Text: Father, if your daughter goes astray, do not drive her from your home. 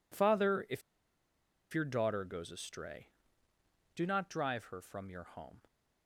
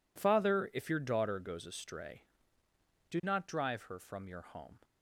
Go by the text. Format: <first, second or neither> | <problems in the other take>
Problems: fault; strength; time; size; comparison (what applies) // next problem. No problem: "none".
second | pauses between "if" and "your"; noticeable; at 0.8 s; 0.92 s long